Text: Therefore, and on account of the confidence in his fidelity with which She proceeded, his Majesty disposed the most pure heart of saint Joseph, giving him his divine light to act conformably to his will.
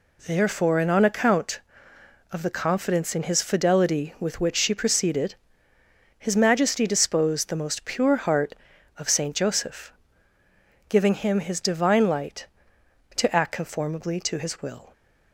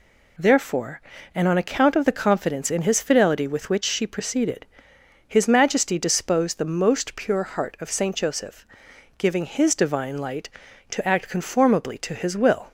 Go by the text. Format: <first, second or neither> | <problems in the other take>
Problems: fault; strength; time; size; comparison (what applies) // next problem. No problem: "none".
first | skips "him"; at 9.4 s